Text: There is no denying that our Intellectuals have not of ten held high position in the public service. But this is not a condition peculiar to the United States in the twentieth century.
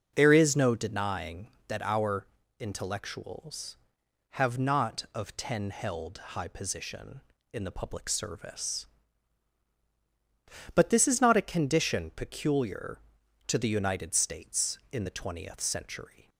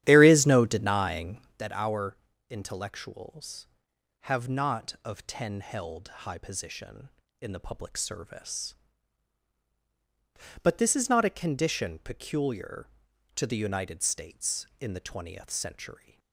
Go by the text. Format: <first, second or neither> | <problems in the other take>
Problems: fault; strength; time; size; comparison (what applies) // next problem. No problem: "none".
first | starts louder than the rest; strong; until 1.6 s; 11.5 dB // pauses between "our" and "Intellectuals"; slight; at 2.1 s; 0.34 s long; slight in the first